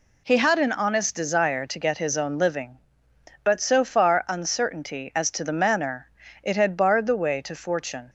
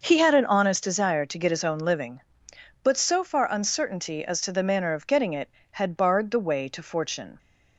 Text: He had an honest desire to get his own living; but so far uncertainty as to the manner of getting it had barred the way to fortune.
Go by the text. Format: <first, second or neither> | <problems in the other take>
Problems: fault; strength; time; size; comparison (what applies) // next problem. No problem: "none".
second | skips "of getting"; at 6.2 s